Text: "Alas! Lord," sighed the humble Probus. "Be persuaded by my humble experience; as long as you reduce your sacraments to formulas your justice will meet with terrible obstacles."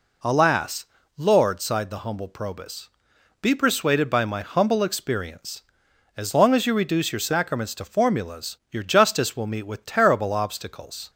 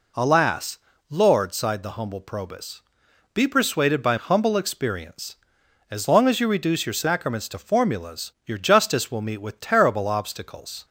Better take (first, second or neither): first